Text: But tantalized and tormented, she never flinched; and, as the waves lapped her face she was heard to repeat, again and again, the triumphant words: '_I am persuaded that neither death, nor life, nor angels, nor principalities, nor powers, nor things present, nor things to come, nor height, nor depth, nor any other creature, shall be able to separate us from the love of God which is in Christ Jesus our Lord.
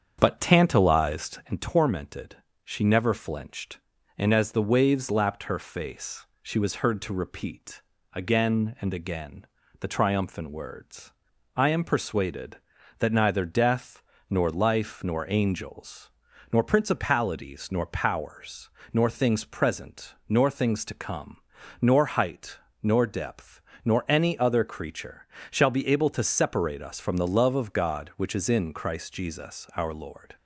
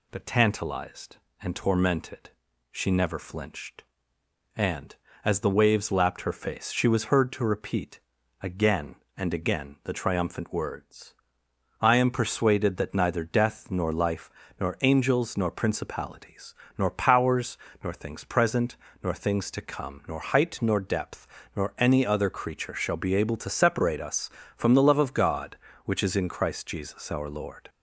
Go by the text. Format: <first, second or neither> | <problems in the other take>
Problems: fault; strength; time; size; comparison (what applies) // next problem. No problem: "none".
second | starts louder than the rest; strong; until 1.6 s; 7.5 dB // pauses between "face" and "she"; slight; at 6.2 s; 0.16 s long